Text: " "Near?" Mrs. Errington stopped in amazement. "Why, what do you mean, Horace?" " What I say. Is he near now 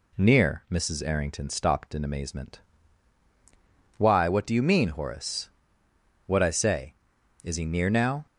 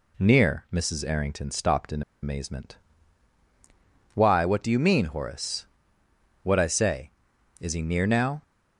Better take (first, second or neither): first